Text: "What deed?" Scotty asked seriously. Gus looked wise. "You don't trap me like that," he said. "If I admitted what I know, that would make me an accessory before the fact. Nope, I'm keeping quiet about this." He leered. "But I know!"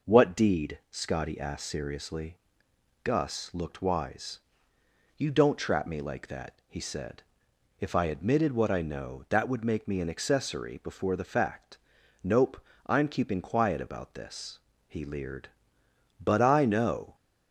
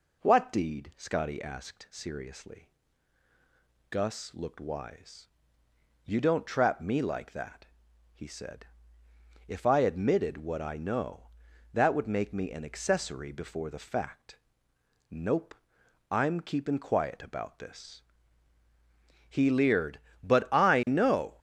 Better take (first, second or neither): neither